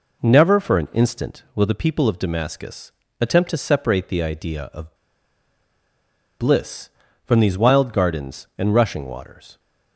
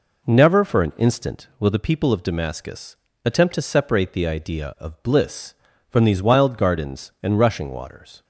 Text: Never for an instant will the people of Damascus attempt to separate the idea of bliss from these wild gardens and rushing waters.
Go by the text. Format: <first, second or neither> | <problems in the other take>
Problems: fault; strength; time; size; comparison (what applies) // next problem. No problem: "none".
second | pauses between "Damascus" and "attempt"; slight; at 2.9 s; 0.30 s long; slight in the second // pauses between "of" and "bliss"; strong; at 4.9 s; 1.4 s long